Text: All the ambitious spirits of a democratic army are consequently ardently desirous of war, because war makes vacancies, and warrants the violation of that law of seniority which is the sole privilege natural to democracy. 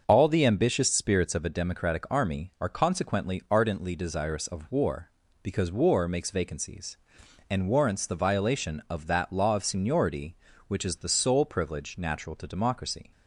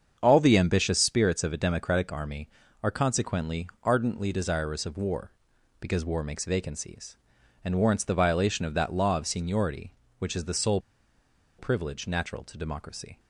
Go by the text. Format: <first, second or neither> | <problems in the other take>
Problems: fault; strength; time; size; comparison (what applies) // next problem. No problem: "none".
first | starts louder than the rest; strong; until 1.2 s; 7 dB; also in the first // pauses between "consequently" and "ardently"; slight; at 3.6 s; 0.16 s long // pauses between "sole" and "privilege"; noticeable; at 10.7 s; 0.78 s long